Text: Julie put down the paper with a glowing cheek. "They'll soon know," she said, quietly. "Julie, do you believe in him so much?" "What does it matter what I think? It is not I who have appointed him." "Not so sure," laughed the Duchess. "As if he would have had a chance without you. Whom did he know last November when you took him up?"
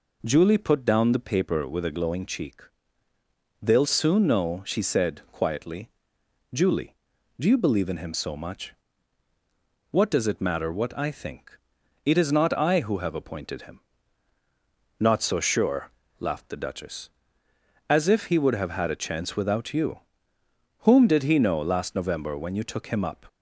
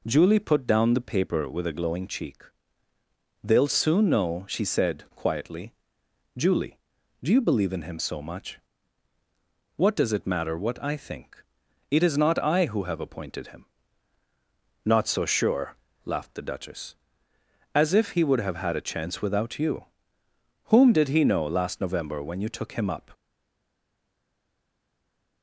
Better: first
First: none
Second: stays silent after the last word; from 23.1 s on; 2.3 s long

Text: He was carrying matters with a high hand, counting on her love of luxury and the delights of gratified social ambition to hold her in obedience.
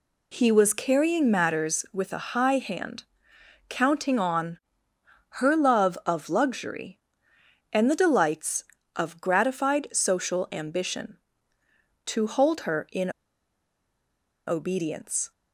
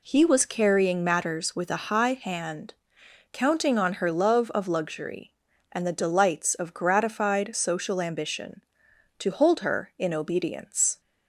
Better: second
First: pauses between "on" and "her"; noticeable; at 4.5 s; 0.84 s long // pauses between "in" and "obedience"; strong; at 13.1 s; 1.3 s long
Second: none

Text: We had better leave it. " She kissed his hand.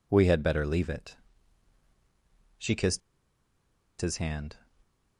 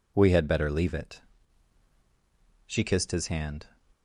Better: second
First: pauses between "kissed" and "his"; at 3.0 s; 1.0 s long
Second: none

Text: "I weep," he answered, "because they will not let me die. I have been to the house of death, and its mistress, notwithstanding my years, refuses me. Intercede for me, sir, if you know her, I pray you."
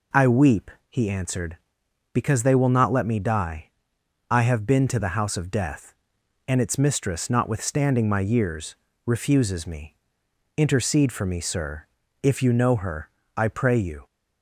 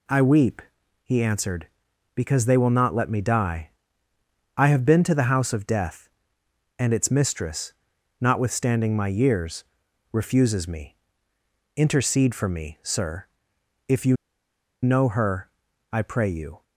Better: first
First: none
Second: pauses between "you" and "know"; noticeable; at 14.1 s; 0.66 s long

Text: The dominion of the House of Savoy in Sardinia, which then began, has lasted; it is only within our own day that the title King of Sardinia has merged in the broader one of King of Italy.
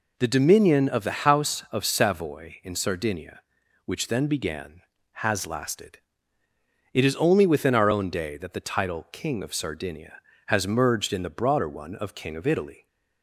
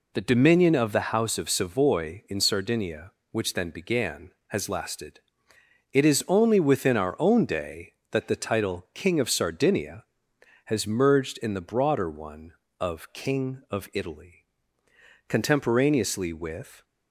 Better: first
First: none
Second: goes on to say "Contemporaneously with"; from 15.2 s on; 1.5 s long

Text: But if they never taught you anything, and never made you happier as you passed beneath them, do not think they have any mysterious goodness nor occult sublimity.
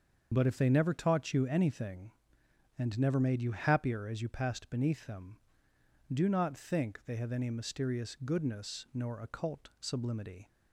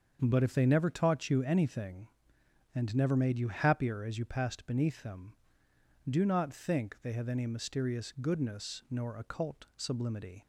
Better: second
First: loses the start of "But"; at 0.3 s; 85 ms // starts louder than the rest; until 1.3 s; 6.5 dB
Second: starts louder than the rest; until 1.2 s; 7 dB

